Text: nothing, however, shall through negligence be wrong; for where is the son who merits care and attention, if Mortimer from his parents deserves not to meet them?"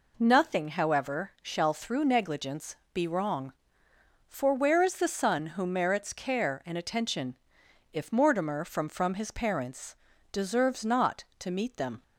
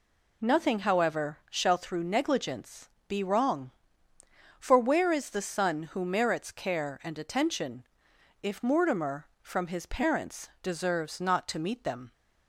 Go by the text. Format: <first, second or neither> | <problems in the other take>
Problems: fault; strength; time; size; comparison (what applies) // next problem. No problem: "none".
second | pauses between "negligence" and "be"; slight; at 2.7 s; 0.18 s long; slight in the second // says "from" twice; at 8.8 s // pauses between "parents" and "deserves"; slight; at 9.9 s; 0.34 s long